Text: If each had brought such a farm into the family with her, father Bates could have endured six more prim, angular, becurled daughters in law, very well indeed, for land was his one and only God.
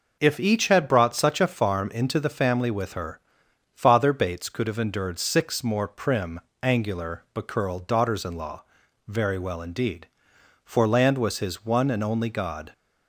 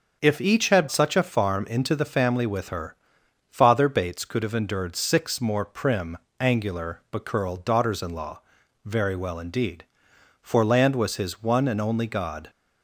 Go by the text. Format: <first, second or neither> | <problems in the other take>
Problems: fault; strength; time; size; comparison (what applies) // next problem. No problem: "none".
first | starts louder than the rest; until 1.2 s; 6.5 dB // skips "brought"; at 0.8 s